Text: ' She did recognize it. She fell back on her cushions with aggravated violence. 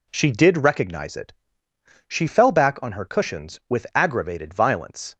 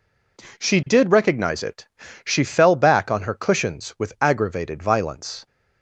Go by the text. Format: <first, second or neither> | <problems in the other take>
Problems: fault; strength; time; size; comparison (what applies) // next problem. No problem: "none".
neither | none